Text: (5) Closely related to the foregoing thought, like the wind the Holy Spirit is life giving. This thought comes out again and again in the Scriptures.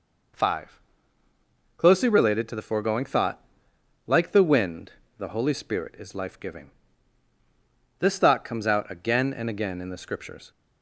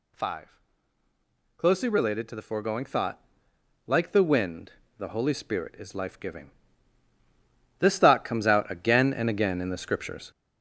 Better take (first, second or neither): first